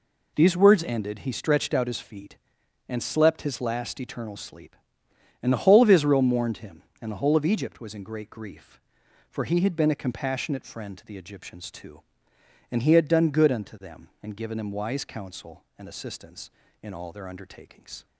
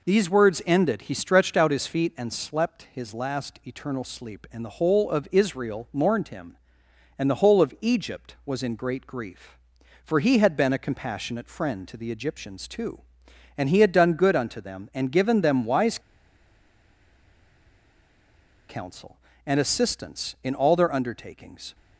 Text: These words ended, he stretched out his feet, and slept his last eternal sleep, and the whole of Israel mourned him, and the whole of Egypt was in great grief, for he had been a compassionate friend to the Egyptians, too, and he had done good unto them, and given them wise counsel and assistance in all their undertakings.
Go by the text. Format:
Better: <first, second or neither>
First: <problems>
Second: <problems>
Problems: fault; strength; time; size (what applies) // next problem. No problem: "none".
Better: first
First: none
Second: pauses between "wise" and "counsel"; strong; at 15.9 s; 2.7 s long